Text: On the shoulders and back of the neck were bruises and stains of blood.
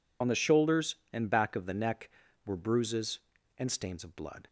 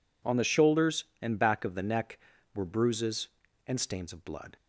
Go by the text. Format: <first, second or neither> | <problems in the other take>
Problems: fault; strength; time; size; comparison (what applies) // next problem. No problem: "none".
second | loses the start of "On"; at 0.2 s; 45 ms